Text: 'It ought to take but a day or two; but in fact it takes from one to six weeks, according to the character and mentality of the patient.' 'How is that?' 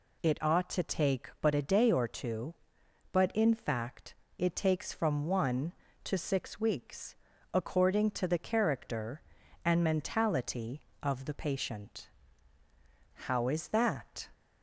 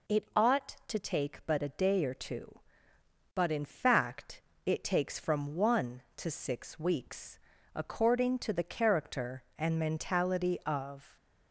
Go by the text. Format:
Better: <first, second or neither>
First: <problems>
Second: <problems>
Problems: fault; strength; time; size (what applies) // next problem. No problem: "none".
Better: first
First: pauses between "fact" and "it"; slight; at 4.1 s; 0.22 s long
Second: pauses between "fact" and "it"; slight; at 4.4 s; 0.24 s long // stops before "the patient How is that"; at 11.1 s